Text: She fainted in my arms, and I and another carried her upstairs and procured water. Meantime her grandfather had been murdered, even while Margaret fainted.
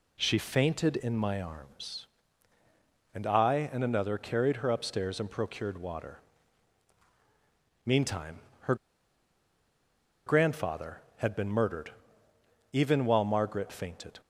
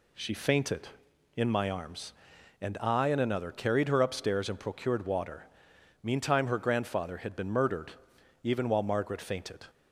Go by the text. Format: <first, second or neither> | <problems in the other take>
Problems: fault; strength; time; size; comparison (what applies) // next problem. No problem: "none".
second | pauses between "Meantime" and "her"; slight; at 8.4 s; 0.22 s long // pauses between "her" and "grandfather"; strong; at 8.7 s; 1.5 s long